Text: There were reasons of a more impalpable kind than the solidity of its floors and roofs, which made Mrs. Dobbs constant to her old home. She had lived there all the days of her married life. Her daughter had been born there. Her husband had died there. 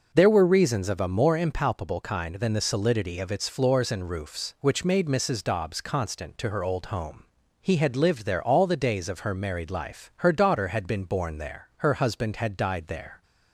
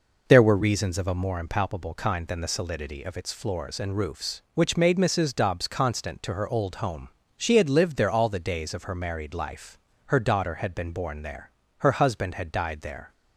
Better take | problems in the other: second | says "He" for "She"; at 7.6 s

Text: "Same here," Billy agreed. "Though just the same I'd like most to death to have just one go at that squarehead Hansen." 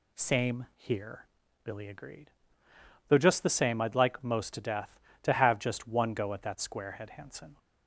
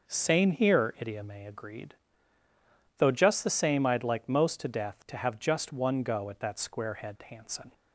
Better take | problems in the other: first | says "Idiome" for "Billy"; at 0.9 s

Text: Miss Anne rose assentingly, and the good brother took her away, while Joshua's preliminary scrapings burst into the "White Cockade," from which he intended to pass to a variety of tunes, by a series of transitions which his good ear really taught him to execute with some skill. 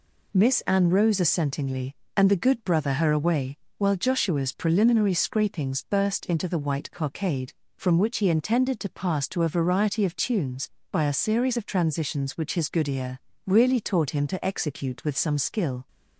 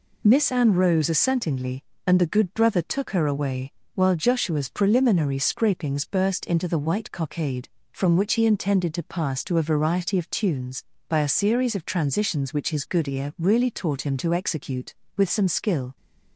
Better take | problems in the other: second | skips "took"; at 2.9 s // pauses between "ear" and "really"; slight; at 13.1 s; 0.30 s long

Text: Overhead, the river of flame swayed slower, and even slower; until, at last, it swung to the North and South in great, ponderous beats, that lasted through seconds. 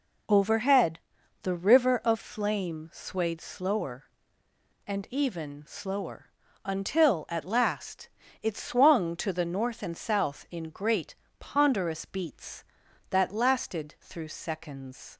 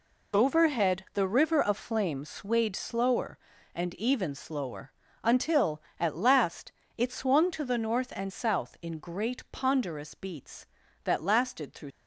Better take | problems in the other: first | stops before "seconds"; at 11.9 s

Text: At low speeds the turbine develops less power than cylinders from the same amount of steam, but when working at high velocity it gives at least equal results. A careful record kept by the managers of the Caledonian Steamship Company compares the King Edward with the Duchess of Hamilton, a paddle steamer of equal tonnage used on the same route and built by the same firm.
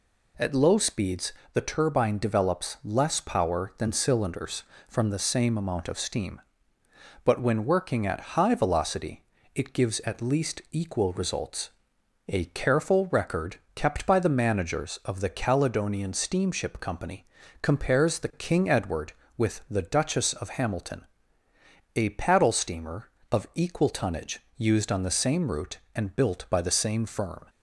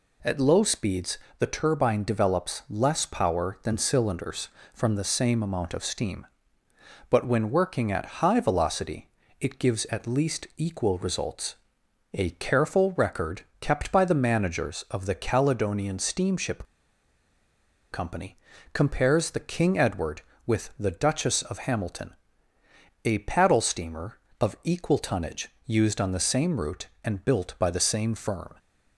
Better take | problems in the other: first | pauses between "speeds" and "the"; slight; at 1.1 s; 0.22 s long; slight in the first // pauses between "velocity" and "it"; slight; at 9.0 s; 0.30 s long; slight in the first // pauses between "record" and "kept"; slight; at 13.4 s; 0.20 s long; slight in the first // pauses between "Steamship" and "Company"; strong; at 16.6 s; 1.2 s long // pauses between "Company" and "compares"; slight; at 18.3 s; 0.36 s long; slight in the first // pauses between "tonnage" and "used"; slight; at 25.4 s; 0.18 s long; slight in the first

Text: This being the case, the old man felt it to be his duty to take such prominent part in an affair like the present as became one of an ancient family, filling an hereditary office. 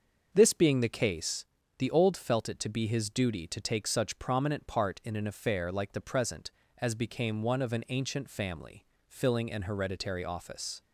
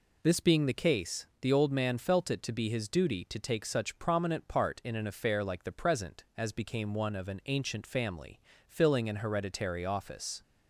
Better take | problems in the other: second | starts louder than the rest; until 1.3 s; 6.5 dB // skips "man"; at 2.1 s

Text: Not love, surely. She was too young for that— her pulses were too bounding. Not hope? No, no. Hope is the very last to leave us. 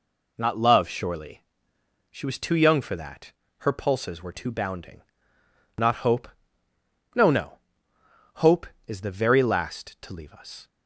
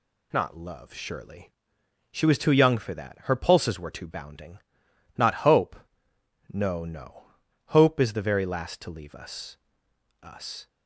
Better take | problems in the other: first | says "us" twice; at 10.2 s

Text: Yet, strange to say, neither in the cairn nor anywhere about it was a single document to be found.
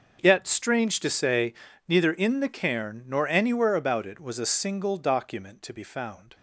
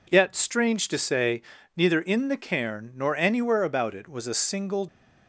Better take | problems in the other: first | stops before "document to be found"; at 4.8 s

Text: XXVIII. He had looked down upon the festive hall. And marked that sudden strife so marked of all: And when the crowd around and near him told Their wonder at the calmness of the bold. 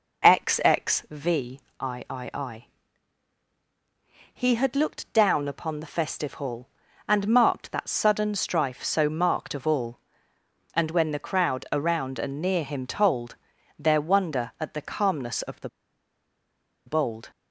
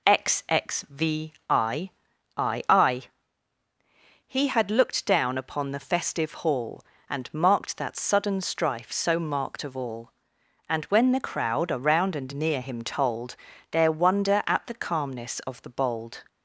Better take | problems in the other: second | pauses between "told" and "Their"; at 13.3 s; 0.42 s long; slight in the second // pauses between "the" and "bold"; at 15.6 s; 1.1 s long

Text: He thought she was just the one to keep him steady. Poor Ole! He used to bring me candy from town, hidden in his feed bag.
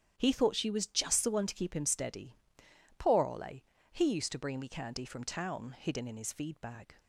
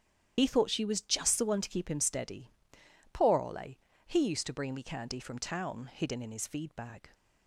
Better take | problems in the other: first | loses the start of "He"; at 0.3 s; 55 ms // starts louder than the rest; strong; until 1.3 s; 9.5 dB; strong in the first

